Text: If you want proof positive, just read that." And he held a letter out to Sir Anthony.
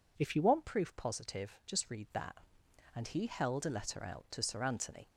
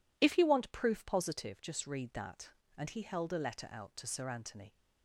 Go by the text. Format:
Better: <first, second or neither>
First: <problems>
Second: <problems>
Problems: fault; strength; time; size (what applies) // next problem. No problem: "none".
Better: neither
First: none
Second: none